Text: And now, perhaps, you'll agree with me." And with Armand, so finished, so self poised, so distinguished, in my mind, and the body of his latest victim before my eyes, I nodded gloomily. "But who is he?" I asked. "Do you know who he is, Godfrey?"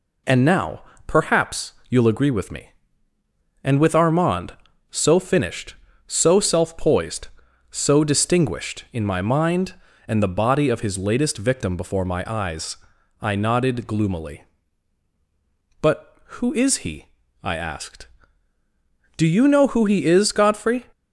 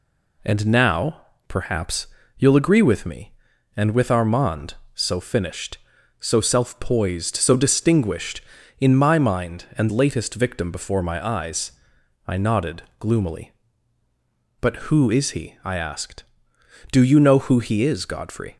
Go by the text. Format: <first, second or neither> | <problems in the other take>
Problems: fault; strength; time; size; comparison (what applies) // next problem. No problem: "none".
first | skips "the body of his"; at 9.8 s // pauses between "nodded" and "gloomily"; slight; at 12.8 s; 0.18 s long